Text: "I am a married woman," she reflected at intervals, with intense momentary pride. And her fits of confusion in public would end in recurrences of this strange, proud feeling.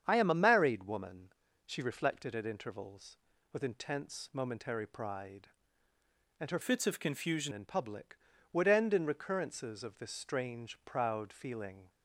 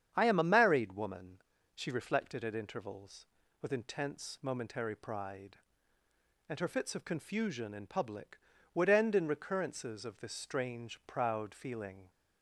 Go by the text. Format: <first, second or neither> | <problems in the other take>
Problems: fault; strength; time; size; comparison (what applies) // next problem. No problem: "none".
second | starts louder than the rest; strong; until 1.0 s; 8 dB; strong in the second // changes voice from "fits" to "confusion"; from 6.6 to 7.5 s; 0.9 s long